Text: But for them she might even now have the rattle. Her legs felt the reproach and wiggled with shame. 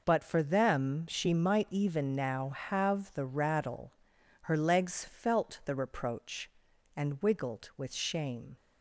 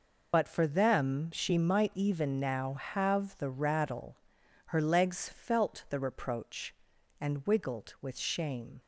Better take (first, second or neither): first